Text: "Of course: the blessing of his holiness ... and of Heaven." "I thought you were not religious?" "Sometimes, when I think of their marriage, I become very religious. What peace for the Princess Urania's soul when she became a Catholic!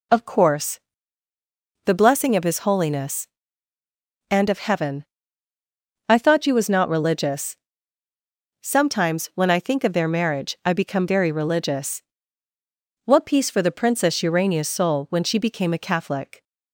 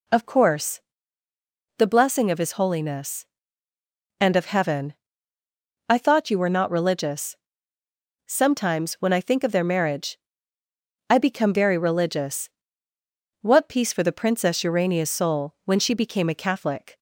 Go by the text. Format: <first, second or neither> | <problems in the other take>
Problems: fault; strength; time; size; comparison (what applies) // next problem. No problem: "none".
second | says "was" for "were"; at 6.5 s